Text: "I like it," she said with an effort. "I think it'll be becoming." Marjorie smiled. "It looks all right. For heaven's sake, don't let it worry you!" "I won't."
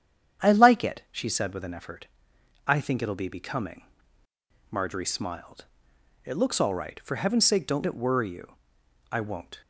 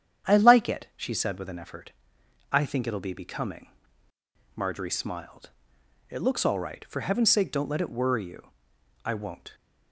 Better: second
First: starts louder than the rest; strong; until 1.5 s; 9 dB // skips "let"; at 7.8 s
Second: starts louder than the rest; strong; until 1.3 s; 9 dB

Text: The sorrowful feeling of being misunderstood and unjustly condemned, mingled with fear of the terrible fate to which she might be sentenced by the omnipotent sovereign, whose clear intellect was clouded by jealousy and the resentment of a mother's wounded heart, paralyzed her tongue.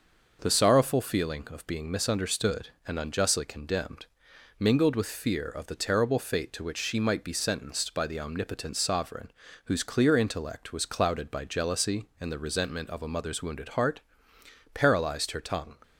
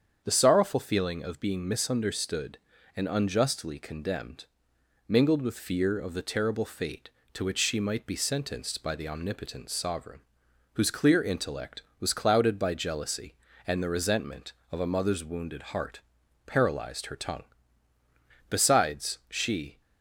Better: first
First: none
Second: starts louder than the rest; strong; until 1.2 s; 7.5 dB // goes on to say "Besides she"; from 18.4 s on; 1.3 s long

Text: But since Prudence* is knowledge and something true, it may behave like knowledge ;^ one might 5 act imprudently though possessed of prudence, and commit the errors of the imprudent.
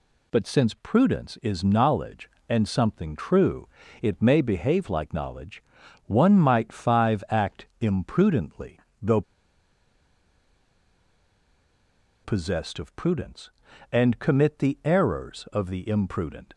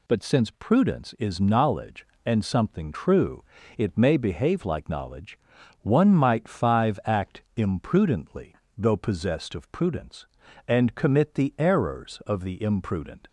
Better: second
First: pauses between "imprudently" and "though"; slight; at 8.7 s; 0.24 s long // pauses between "though" and "possessed"; strong; at 9.2 s; 3.0 s long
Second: pauses between "imprudently" and "though"; slight; at 8.5 s; 0.24 s long

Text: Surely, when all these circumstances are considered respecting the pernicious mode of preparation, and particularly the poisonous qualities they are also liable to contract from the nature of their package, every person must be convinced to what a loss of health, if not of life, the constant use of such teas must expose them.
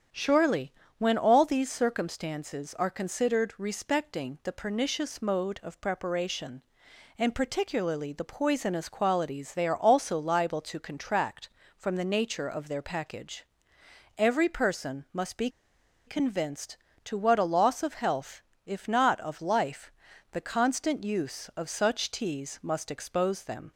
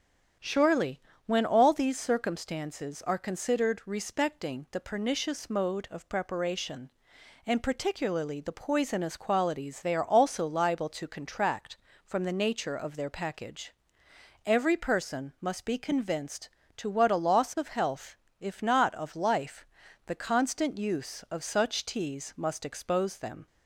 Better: second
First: starts louder than the rest; strong; until 1.3 s; 8.5 dB // pauses between "be" and "convinced"; noticeable; at 15.4 s; 0.58 s long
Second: starts louder than the rest; strong; until 1.6 s; 8.5 dB

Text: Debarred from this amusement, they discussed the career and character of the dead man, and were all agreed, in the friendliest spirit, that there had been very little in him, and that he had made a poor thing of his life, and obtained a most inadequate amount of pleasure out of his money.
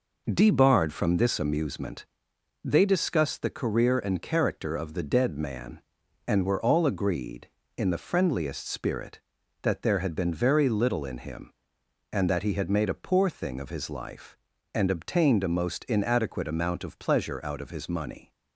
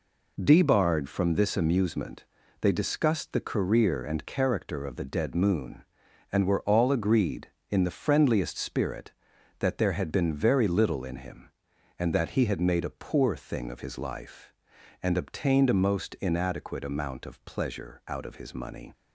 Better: first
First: none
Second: says "moon" for "man"; at 5.3 s

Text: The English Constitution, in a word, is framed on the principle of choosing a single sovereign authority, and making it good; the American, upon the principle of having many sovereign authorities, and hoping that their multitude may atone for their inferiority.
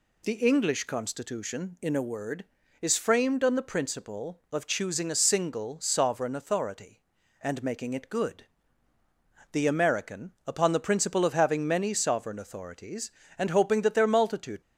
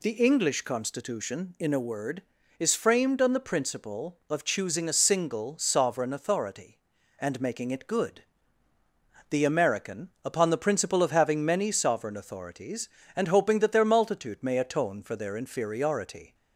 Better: second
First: stops before "may atone for their inferiority"; at 14.6 s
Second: none

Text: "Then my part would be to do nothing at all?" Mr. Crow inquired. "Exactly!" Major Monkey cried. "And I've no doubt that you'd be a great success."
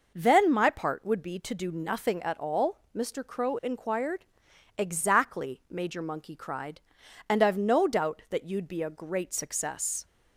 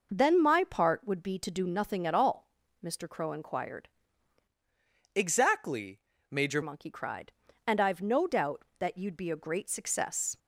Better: first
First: none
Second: changes voice from "Exactly" to "Major"; from 5.1 to 6.6 s; 1.5 s long

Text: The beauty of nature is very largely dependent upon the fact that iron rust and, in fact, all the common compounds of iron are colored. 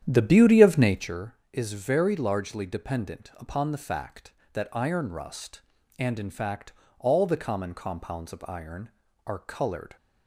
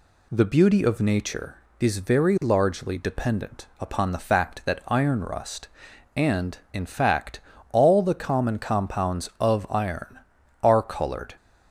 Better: second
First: starts louder than the rest; strong; until 1.2 s; 10 dB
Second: none

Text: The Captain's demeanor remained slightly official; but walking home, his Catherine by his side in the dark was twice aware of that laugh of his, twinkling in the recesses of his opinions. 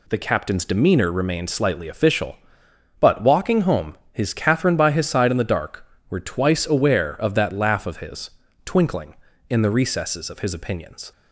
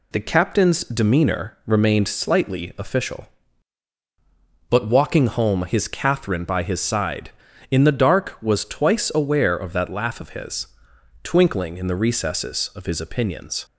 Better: second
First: says "were" for "was"; at 6.0 s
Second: none

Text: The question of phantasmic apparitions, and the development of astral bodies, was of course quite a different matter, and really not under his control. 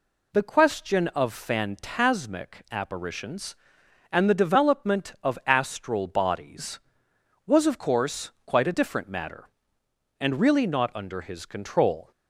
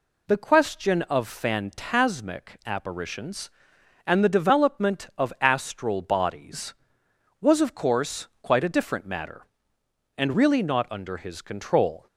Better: neither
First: pauses between "course" and "quite"; slight; at 8.2 s; 0.16 s long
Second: pauses between "course" and "quite"; slight; at 8.2 s; 0.16 s long

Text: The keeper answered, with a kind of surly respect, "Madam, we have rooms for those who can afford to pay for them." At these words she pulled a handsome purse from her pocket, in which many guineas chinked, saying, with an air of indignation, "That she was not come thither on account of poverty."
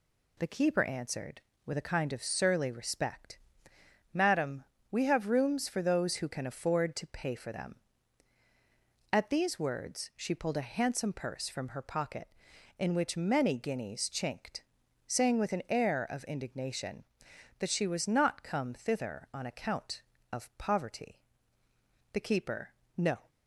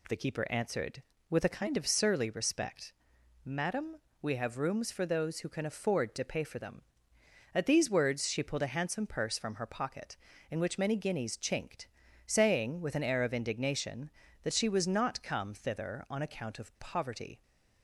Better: second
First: goes on to say "The keeper no"; noticeable; from 22.1 s on; 1.1 s long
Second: none

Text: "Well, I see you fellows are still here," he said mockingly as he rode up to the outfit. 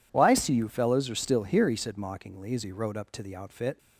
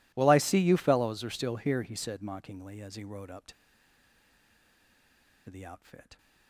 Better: first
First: none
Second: pauses between "to" and "the"; strong; at 3.5 s; 1.9 s long

